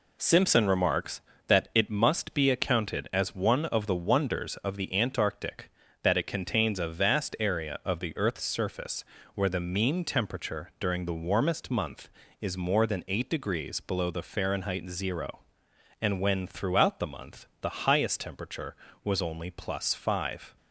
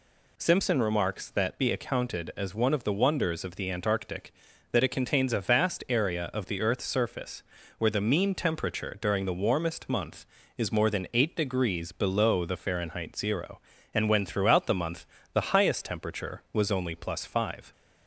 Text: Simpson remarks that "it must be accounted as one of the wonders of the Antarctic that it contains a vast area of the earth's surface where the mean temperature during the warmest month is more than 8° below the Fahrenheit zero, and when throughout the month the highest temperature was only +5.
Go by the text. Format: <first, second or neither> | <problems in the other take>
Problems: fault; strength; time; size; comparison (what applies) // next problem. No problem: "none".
first | skips "it must"; at 1.5 s // pauses between "surface" and "where"; slight; at 7.4 s; 0.34 s long; slight in the first // pauses between "month" and "the"; slight; at 15.0 s; 0.28 s long